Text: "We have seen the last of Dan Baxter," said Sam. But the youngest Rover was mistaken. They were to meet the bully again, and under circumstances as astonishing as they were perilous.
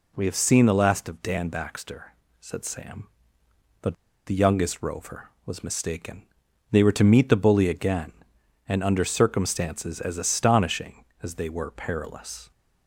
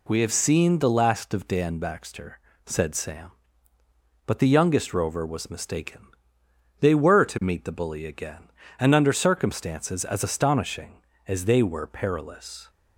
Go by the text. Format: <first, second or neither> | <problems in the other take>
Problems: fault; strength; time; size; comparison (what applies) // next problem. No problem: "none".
second | pauses between "But" and "the"; slight; at 3.9 s; 0.31 s long